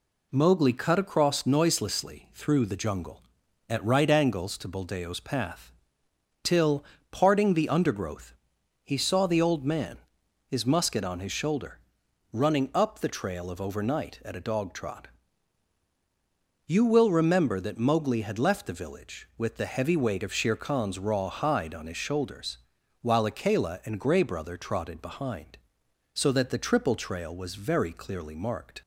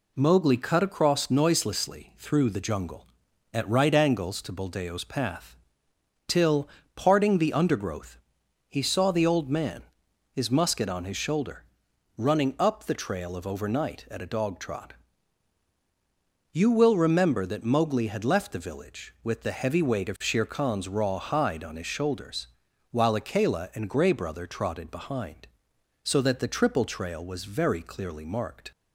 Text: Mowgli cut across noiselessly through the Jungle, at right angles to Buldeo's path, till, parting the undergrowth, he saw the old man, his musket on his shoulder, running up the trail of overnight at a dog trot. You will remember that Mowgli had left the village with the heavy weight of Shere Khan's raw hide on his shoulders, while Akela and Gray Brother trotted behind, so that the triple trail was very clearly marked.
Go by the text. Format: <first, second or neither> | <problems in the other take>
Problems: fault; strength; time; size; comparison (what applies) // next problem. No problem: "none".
neither | none